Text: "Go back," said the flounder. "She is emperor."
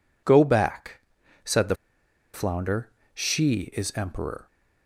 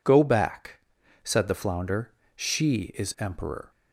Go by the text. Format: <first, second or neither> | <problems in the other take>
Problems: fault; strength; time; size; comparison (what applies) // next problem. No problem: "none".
second | pauses between "the" and "flounder"; noticeable; at 1.7 s; 0.58 s long